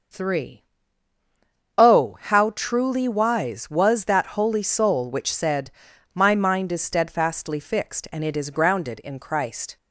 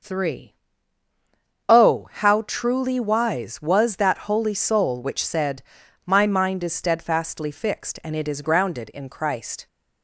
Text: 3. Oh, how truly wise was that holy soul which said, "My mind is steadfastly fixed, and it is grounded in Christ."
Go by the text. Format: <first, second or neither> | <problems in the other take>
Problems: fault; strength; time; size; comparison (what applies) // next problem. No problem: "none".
neither | none